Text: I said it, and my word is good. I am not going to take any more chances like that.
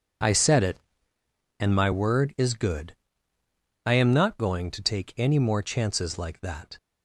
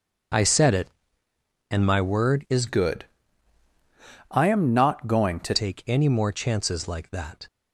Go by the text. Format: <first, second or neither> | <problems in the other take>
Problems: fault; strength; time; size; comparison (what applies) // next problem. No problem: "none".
first | starts louder than the rest; until 2.1 s; 6.5 dB // changes voice from "good" to "to"; from 2.6 to 5.5 s; 2.9 s long